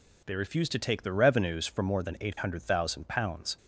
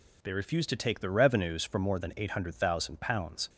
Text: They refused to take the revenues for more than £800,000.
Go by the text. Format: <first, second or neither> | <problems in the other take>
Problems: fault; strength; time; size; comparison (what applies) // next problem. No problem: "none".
neither | none